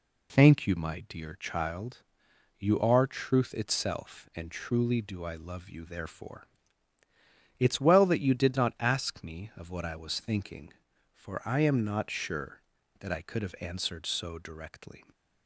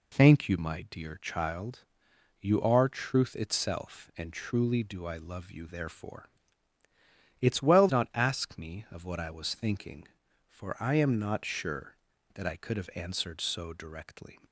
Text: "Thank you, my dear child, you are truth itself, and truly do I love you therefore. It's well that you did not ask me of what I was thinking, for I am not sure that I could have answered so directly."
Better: first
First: none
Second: skips "that you did"; at 7.8 s

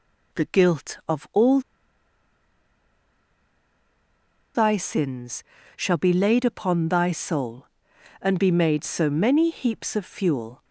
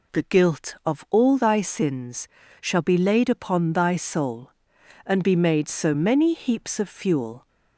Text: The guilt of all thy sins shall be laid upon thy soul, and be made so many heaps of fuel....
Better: second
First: pauses between "all" and "thy"; strong; at 1.5 s; 2.9 s long // pauses between "sins" and "shall"; slight; at 5.4 s; 0.34 s long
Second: pauses between "sins" and "shall"; slight; at 2.2 s; 0.34 s long

